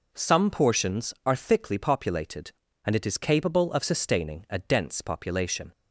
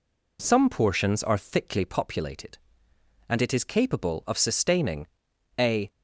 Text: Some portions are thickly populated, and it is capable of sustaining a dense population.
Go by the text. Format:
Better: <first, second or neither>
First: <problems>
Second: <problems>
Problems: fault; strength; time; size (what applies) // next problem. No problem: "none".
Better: first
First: none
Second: pauses between "sustaining" and "a"; noticeable; at 5.0 s; 0.52 s long // stops before "dense population"; at 5.9 s